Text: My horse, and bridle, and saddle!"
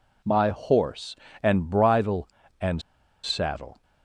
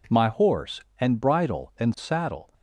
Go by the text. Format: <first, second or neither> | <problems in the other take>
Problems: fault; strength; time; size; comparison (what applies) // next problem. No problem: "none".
second | pauses between "and" and "saddle"; at 2.8 s; 0.43 s long